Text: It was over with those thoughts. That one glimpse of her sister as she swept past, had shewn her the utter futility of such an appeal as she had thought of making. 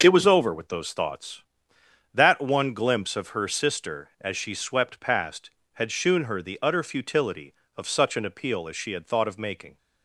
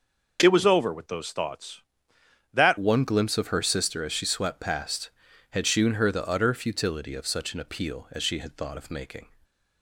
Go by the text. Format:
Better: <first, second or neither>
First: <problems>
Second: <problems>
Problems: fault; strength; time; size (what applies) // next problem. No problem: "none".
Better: first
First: none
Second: starts louder than the rest; noticeable; until 1.4 s; 6 dB // changes voice at "one"; from 2.7 s on; 6.5 s long // stays silent after the last word; slight; from 9.2 s on; 0.6 s long